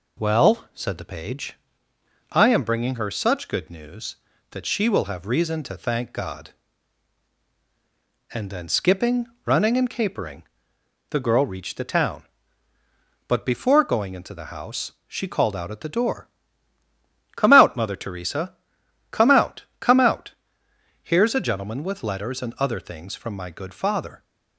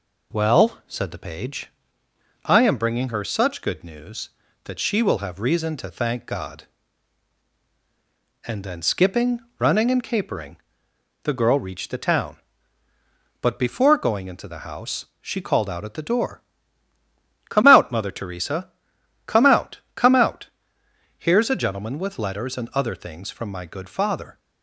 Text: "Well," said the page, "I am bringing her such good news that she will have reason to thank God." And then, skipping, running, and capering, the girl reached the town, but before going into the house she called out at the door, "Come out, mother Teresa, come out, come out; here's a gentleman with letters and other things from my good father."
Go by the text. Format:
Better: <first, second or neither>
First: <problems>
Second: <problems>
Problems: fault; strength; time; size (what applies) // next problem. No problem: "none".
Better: neither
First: none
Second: none